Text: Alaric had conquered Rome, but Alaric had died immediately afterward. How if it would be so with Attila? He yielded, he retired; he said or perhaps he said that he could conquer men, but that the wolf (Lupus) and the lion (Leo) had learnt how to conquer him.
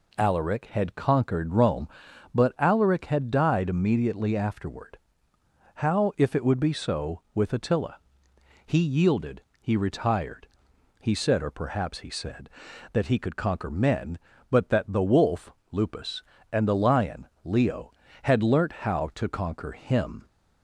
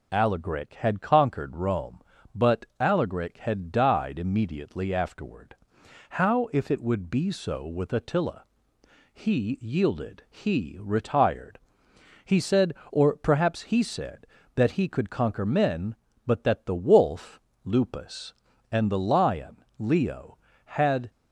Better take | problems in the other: first | stops before "learnt how to conquer him"; at 21.1 s

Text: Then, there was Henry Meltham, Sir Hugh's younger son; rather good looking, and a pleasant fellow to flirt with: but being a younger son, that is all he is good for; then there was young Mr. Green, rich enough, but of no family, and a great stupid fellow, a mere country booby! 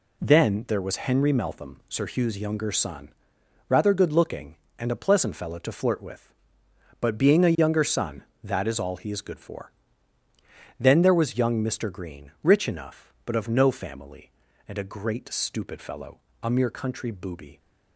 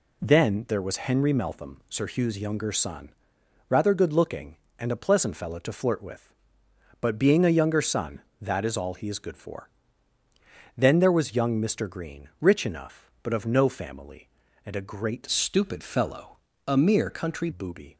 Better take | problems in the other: first | changes voice from "stupid" to "country"; from 15.2 to 17.4 s; 2.2 s long

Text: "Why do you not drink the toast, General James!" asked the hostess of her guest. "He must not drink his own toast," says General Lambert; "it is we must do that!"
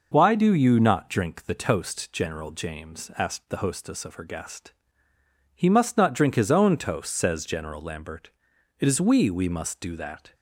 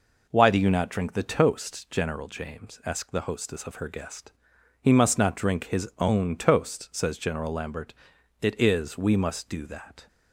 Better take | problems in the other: second | says "we" twice; at 9.3 s

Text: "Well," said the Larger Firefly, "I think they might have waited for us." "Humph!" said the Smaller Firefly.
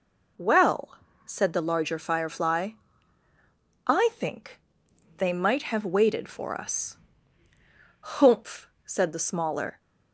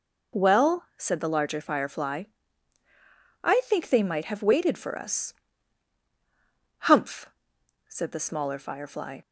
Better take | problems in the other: second | pauses between "think" and "they"; noticeable; at 4.5 s; 0.58 s long // stops before "Firefly"; at 9.7 s

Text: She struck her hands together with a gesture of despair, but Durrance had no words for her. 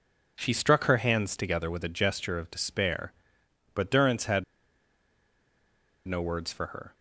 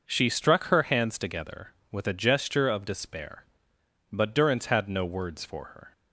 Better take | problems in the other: second | pauses between "had" and "no"; strong; at 4.4 s; 1.6 s long

